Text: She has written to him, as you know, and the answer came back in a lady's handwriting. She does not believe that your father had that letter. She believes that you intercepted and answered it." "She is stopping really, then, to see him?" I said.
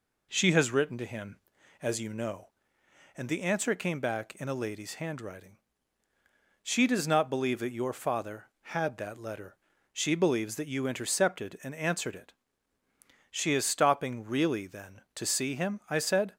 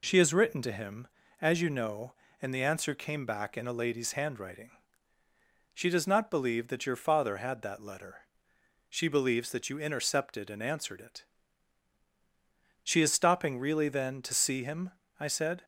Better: neither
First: none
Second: none

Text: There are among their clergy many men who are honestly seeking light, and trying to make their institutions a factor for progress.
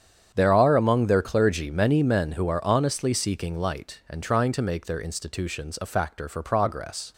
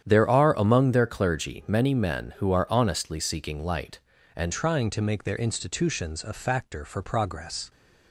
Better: first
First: starts louder than the rest; strong; until 1.3 s; 8.5 dB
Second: starts louder than the rest; strong; until 1.0 s; 9 dB // changes voice at "trying"; from 4.5 s on; 3.1 s long

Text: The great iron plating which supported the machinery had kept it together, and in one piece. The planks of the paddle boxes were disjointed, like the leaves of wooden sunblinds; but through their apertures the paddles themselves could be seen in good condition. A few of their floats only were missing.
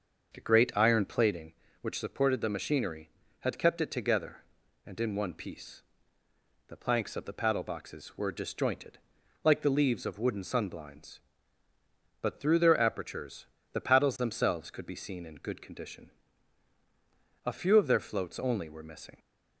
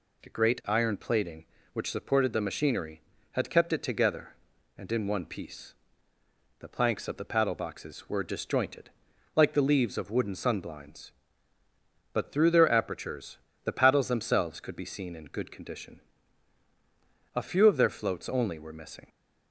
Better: second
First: starts louder than the rest; until 1.5 s; 6 dB // pauses between "apertures" and "the"; slight; at 13.4 s; 0.28 s long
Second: pauses between "apertures" and "the"; slight; at 13.3 s; 0.28 s long

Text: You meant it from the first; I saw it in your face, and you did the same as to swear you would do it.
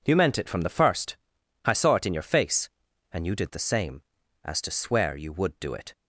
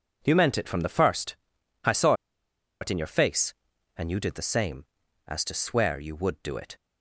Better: first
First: none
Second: pauses between "saw" and "it"; noticeable; at 2.1 s; 0.67 s long

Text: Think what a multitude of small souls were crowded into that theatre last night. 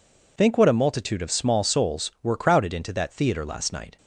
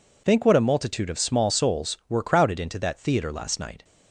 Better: neither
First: none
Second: none

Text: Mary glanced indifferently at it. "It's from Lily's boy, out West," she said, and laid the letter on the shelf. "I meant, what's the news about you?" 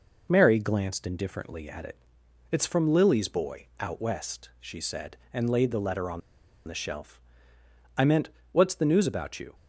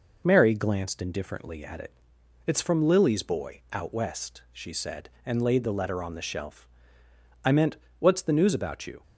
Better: second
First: pauses between "on" and "the"; noticeable; at 6.2 s; 0.46 s long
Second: none

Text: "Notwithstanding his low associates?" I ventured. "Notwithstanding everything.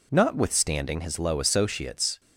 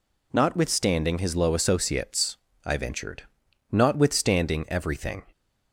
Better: second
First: stops before "I ventured Notwithstanding everything"; at 2.1 s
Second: none

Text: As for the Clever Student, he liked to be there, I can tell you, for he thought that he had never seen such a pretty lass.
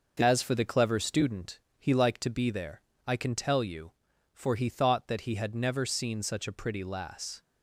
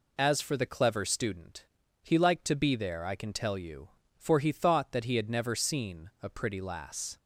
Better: first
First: none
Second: skips "such"; at 6.1 s

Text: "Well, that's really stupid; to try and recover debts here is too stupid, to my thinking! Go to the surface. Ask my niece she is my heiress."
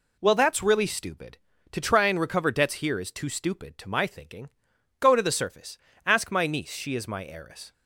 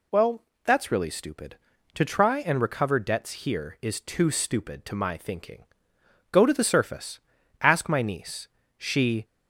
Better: first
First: none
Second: pauses between "niece" and "she"; slight; at 8.4 s; 0.30 s long // stops before "is my heiress"; at 9.2 s

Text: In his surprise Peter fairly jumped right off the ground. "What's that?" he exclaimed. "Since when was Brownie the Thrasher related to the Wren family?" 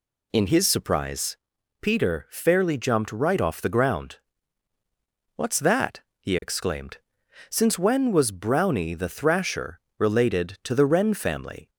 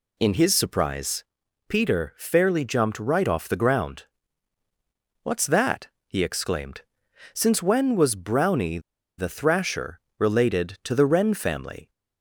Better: first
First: pauses between "surprise" and "Peter"; noticeable; at 1.3 s; 0.46 s long // pauses between "Thrasher" and "related"; slight; at 9.7 s; 0.20 s long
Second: pauses between "surprise" and "Peter"; noticeable; at 1.2 s; 0.46 s long // pauses between "Brownie" and "the"; at 8.7 s; 0.38 s long // pauses between "Thrasher" and "related"; slight; at 9.9 s; 0.20 s long

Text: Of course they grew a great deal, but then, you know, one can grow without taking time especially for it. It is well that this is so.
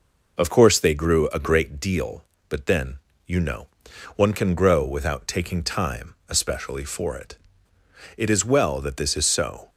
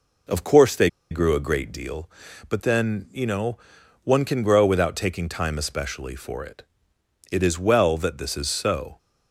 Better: first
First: none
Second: pauses between "they" and "grew"; slight; at 0.8 s; 0.22 s long

